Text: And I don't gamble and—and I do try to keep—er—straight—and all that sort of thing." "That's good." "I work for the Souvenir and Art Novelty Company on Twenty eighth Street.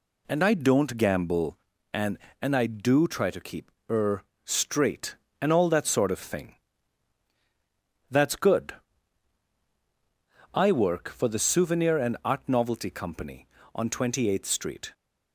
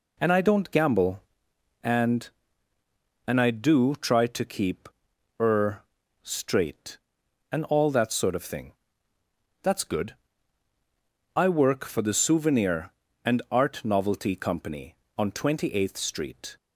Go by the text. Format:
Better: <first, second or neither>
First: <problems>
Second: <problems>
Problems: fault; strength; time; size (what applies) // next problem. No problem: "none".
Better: neither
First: none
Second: none